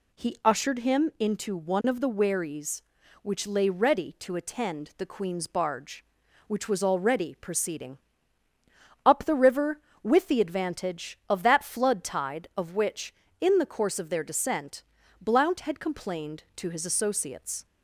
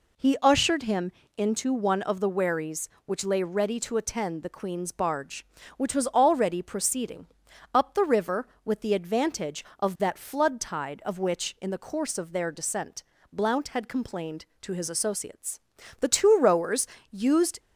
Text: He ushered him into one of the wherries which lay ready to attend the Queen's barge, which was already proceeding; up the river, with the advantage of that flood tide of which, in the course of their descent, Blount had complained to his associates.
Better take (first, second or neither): first